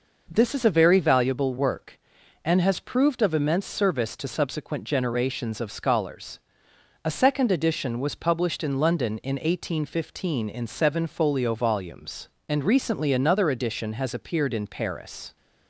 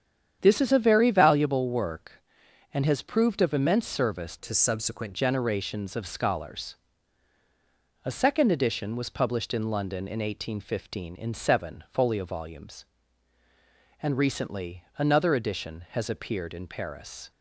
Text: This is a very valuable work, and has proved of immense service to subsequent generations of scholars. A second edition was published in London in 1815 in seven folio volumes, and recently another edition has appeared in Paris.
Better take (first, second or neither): first